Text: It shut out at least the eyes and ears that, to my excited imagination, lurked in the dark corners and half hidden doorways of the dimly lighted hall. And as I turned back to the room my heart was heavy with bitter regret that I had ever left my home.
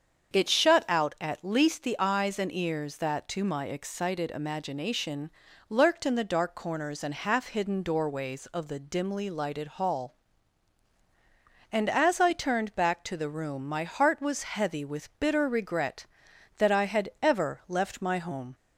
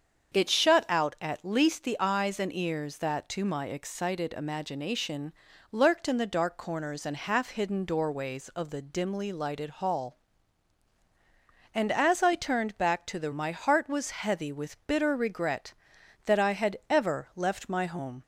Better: first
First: starts louder than the rest; strong; until 1.3 s; 7 dB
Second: starts louder than the rest; strong; until 1.4 s; 7 dB // skips "room"; at 13.3 s

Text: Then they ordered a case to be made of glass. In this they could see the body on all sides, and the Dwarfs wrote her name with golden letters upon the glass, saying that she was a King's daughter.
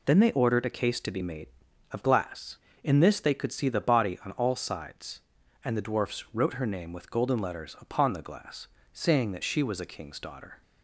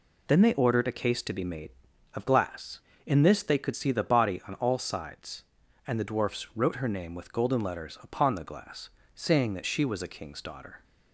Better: neither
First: none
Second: none

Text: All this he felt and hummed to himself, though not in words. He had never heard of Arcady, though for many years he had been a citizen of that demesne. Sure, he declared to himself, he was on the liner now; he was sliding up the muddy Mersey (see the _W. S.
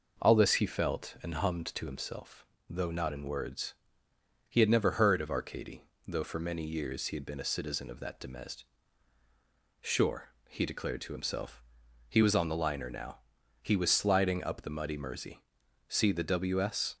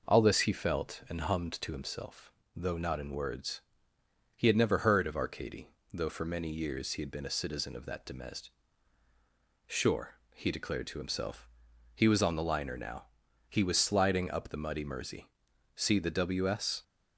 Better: neither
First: none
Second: none

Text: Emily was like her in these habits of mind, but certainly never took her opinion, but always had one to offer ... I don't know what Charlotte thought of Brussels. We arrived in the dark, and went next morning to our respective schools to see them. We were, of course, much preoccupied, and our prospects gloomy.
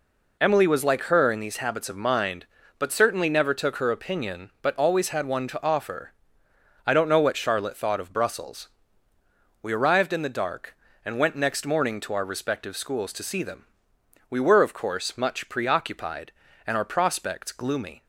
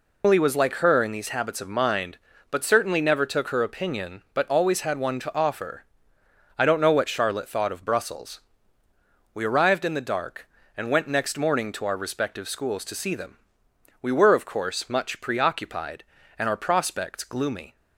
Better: first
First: none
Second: loses the start of "Emily"; at 0.2 s; 130 ms

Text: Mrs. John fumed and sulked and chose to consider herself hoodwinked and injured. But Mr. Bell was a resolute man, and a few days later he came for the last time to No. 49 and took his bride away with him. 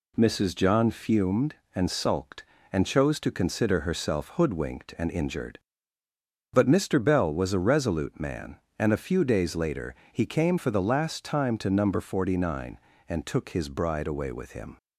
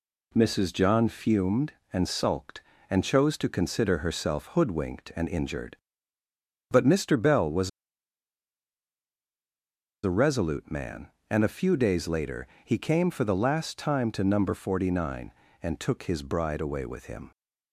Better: first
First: pauses between "later" and "he"; slight; at 9.9 s; 0.16 s long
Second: pauses between "was" and "a"; strong; at 7.6 s; 2.3 s long // pauses between "later" and "he"; slight; at 12.4 s; 0.16 s long

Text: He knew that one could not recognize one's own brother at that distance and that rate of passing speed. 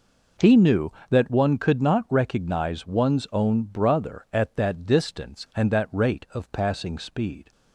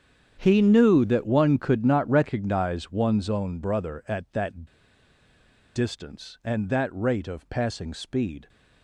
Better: first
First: none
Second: starts louder than the rest; strong; until 1.4 s; 8.5 dB // pauses between "that" and "distance"; at 4.6 s; 1.1 s long

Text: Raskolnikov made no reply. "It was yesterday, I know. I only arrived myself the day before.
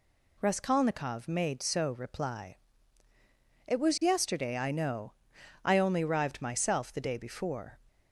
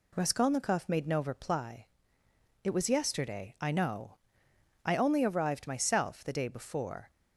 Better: second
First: says "so" for "no"; at 1.6 s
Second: none

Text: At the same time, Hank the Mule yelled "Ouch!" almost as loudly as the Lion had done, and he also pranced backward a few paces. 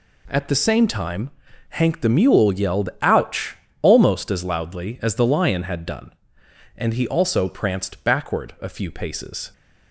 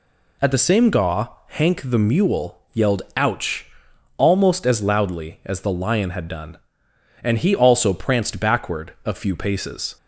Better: first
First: none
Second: says "gaw" for "time"; at 0.8 s

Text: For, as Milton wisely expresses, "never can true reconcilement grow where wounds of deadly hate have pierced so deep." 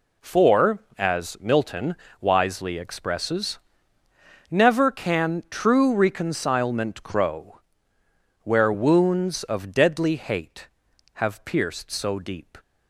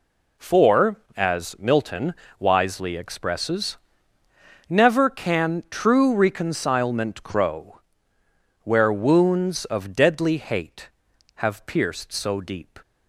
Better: neither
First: pauses between "Milton" and "wisely"; slight; at 1.9 s; 0.24 s long // pauses between "grow" and "where"; noticeable; at 7.5 s; 0.84 s long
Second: pauses between "Milton" and "wisely"; slight; at 2.1 s; 0.24 s long // pauses between "grow" and "where"; noticeable; at 7.8 s; 0.84 s long

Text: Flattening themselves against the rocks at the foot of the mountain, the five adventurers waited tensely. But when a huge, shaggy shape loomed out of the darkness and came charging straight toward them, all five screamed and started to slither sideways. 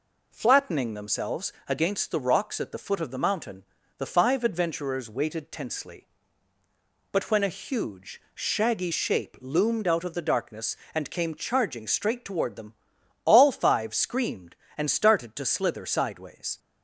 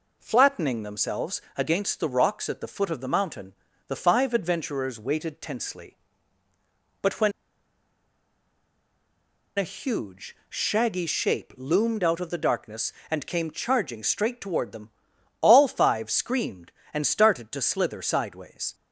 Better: first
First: pauses between "themselves" and "against"; slight; at 1.5 s; 0.16 s long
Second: pauses between "themselves" and "against"; slight; at 1.3 s; 0.16 s long // pauses between "when" and "a"; strong; at 7.3 s; 2.2 s long

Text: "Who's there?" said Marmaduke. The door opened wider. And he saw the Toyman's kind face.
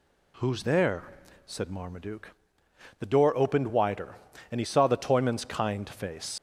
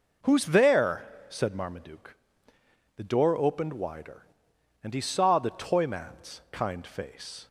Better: second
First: leaves "face" unfinished; at 6.3 s; 65 ms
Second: none

